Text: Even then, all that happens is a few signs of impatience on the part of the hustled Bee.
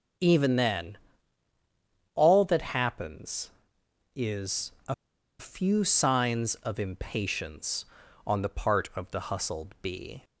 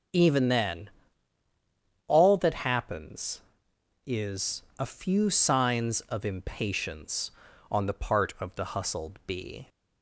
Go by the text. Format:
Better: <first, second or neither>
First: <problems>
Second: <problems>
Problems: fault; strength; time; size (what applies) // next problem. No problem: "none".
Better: second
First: starts louder than the rest; until 2.3 s; 7 dB // pauses between "is" and "a"; slight; at 4.7 s; 0.16 s long // pauses between "a" and "few"; noticeable; at 4.9 s; 0.46 s long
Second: starts louder than the rest; until 2.3 s; 7 dB // pauses between "is" and "a"; slight; at 4.6 s; 0.16 s long